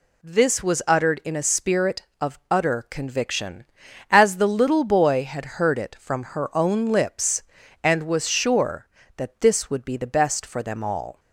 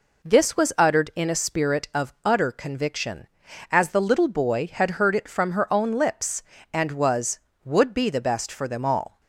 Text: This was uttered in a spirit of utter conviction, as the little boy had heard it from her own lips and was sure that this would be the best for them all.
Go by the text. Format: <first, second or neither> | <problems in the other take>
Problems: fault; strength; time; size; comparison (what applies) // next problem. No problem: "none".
first | skips "sure that this"; at 7.5 s